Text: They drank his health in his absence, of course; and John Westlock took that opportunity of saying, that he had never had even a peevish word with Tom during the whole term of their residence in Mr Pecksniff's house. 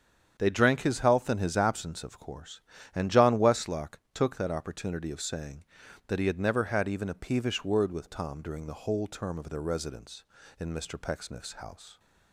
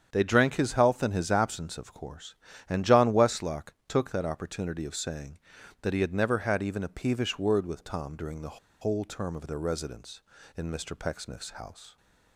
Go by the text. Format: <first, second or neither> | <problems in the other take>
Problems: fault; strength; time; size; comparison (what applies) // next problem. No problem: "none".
first | starts louder than the rest; strong; until 1.1 s; 8 dB; strong in the first // pauses between "Westlock" and "took"; slight; at 3.7 s; 0.16 s long; slight in the first // pauses between "the" and "whole"; slight; at 8.5 s; 0.23 s long